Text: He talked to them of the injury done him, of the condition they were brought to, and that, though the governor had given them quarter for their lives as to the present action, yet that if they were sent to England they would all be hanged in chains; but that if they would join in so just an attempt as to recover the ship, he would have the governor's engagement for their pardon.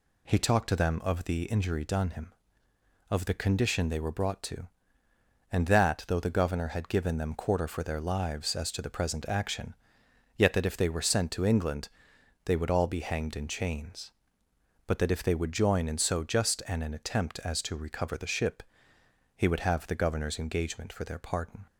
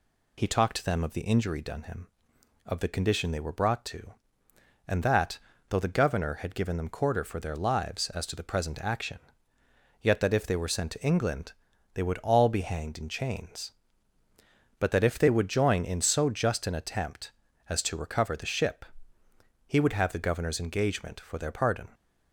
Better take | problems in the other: second | pauses between "England" and "they"; noticeable; at 11.8 s; 0.58 s long; also in the second // says "an" twice; at 16.8 s

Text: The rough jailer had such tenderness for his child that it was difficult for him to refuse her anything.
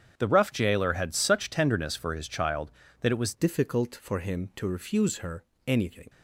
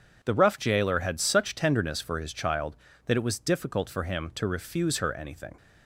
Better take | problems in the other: second | starts louder than the rest; strong; until 1.1 s; 8 dB // changes voice at "difficult"; from 3.3 s on; 2.7 s long // pauses between "her" and "anything"; slight; at 5.4 s; 0.24 s long

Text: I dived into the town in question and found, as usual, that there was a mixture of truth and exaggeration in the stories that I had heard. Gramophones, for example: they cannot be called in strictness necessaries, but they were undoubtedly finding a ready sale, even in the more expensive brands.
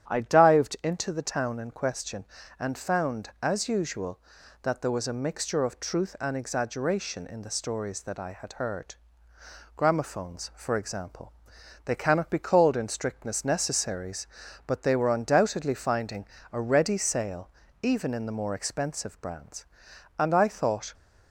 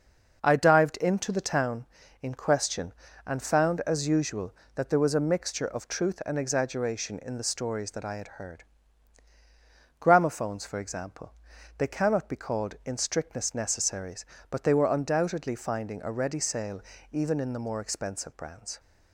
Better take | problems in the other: second | starts louder than the rest; strong; until 1.1 s; 9.5 dB // pauses between "finding" and "a"; slight; at 16.2 s; 0.26 s long // goes on to say "And I thought"; noticeable; from 20.1 s on; 0.74 s long

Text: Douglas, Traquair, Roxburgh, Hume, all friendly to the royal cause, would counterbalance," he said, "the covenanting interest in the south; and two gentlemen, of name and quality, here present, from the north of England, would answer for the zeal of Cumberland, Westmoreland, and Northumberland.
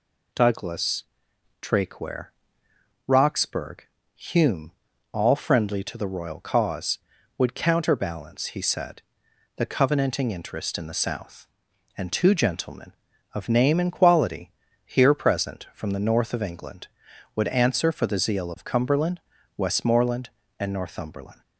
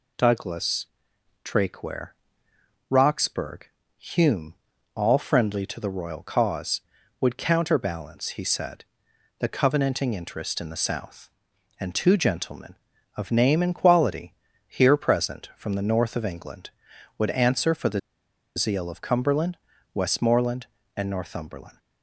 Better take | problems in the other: first | pauses between "the" and "zeal"; noticeable; at 17.9 s; 0.56 s long

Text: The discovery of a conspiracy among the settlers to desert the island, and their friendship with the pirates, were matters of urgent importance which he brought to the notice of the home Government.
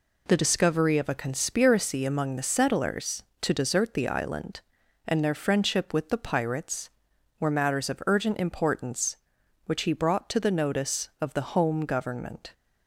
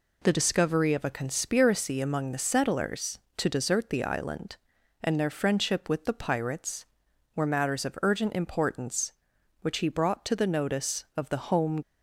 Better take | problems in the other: first | stops before "Government"; at 11.8 s

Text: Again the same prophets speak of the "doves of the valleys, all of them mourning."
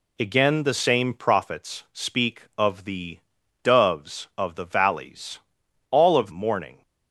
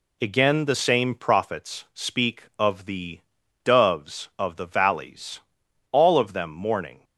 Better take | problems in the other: second | pauses between "the" and "doves"; at 3.1 s; 0.44 s long; also in the second // skips "them"; at 6.3 s

